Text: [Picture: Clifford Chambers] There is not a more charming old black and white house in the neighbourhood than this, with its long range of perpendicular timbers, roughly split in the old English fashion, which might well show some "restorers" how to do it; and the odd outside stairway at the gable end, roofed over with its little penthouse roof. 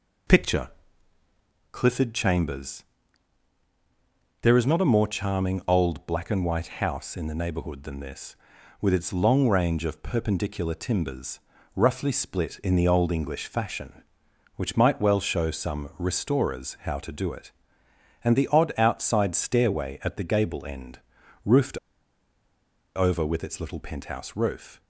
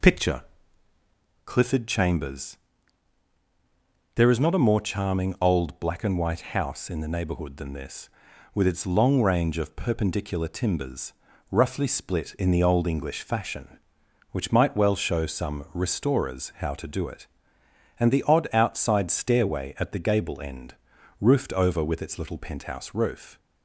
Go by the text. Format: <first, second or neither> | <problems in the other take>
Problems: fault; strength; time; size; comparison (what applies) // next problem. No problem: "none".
second | pauses between "Chambers" and "There"; strong; at 2.8 s; 1.5 s long; strong in the second // pauses between "roofed" and "over"; at 21.7 s; 1.1 s long